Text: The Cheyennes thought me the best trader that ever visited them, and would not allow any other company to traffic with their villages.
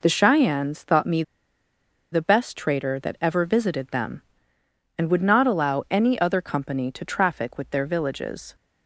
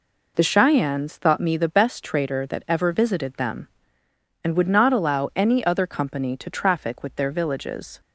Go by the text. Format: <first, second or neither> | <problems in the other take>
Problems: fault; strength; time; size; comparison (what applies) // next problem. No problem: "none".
second | pauses between "me" and "the"; noticeable; at 1.2 s; 0.90 s long